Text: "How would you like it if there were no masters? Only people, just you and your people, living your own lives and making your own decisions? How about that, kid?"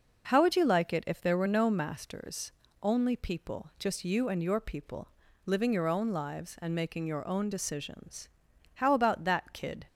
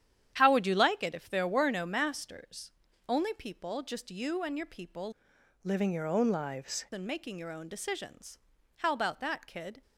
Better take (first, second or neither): first